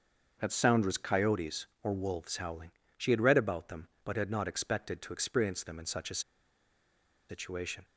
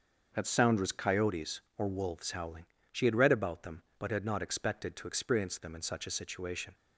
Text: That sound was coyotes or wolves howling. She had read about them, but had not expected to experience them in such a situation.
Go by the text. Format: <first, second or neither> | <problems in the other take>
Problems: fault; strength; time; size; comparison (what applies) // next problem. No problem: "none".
second | starts louder than the rest; until 1.4 s; 6.5 dB; also in the second // pauses between "a" and "situation"; at 6.1 s; 1.0 s long